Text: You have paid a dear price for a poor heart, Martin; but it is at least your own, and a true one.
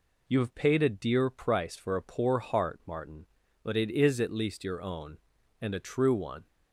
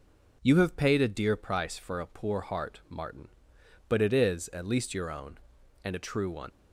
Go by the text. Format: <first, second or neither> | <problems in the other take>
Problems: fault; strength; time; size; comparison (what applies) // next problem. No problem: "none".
first | leaves "one" unfinished; at 6.5 s; 85 ms